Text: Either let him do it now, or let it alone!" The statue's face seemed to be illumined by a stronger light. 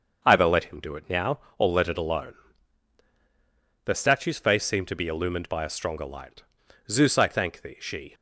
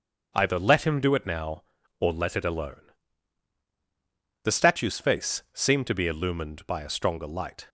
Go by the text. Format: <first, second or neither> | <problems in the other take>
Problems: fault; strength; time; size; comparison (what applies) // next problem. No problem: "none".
second | starts louder than the rest; until 1.2 s; 6.5 dB; also in the second // goes on to say "Zeus I thank thee she"; noticeable; from 6.8 s on; 1.2 s long